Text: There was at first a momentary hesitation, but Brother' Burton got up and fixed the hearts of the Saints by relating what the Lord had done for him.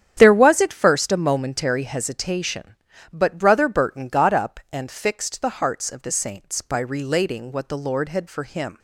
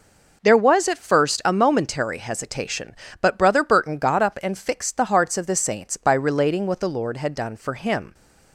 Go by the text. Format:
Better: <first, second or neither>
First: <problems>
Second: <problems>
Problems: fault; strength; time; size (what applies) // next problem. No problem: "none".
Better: second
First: starts louder than the rest; strong; until 1.1 s; 9 dB // skips "done"; at 8.2 s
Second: none